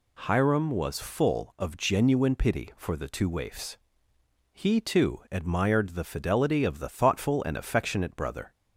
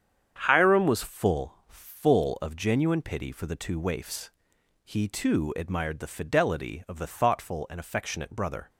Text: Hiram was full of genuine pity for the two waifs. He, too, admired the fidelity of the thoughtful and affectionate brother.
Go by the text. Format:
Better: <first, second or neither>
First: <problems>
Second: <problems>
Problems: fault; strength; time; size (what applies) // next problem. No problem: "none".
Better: first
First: none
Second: starts louder than the rest; strong; until 1.4 s; 8 dB // says "full" twice; at 1.6 s